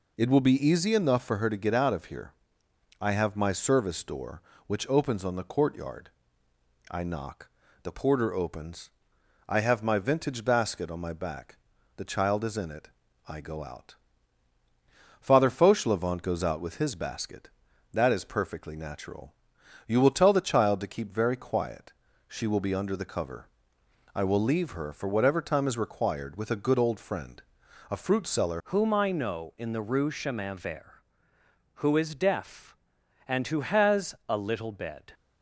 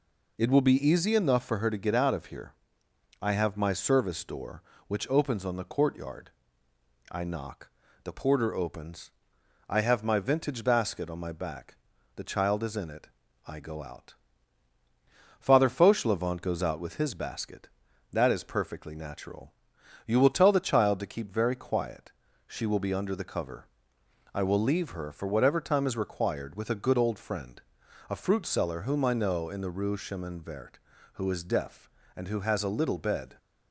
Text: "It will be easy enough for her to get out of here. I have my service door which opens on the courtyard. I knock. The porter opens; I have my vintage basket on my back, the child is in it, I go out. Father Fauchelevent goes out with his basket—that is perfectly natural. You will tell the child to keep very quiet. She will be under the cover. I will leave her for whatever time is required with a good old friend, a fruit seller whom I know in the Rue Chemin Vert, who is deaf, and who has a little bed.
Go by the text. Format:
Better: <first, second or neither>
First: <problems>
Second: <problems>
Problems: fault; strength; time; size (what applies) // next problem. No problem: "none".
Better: second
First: changes voice at "whom"; from 28.6 s on; 6.5 s long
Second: none